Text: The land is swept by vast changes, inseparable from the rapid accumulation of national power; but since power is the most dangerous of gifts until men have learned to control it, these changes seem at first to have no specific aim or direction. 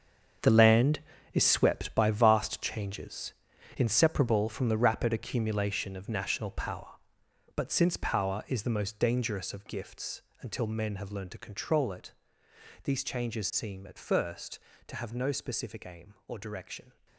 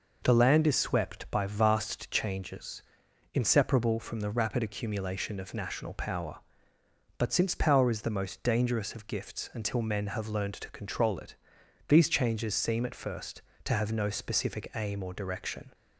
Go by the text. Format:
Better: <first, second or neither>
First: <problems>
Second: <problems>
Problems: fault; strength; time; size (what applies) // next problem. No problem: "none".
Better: second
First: gets quieter; strong; throughout; 11.5 dB // pauses between "gifts" and "until"; slight; at 10.2 s; 0.18 s long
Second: none